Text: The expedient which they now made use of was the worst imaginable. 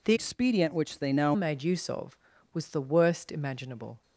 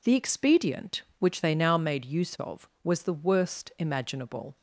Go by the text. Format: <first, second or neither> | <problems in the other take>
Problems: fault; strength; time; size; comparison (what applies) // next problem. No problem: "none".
second | changes voice from "expedient" to "now"; from 0.1 to 1.3 s; 1.2 s long